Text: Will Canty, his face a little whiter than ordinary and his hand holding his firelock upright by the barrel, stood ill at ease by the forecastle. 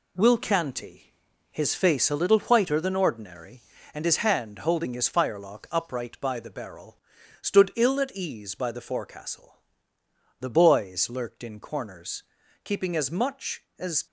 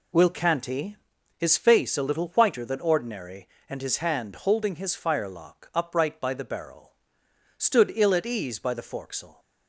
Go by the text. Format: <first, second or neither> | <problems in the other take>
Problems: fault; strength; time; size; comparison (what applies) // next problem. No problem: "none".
second | goes on to say "The boys lurked in corners keeping as much as"; strong; from 10.3 s on; 3.6 s long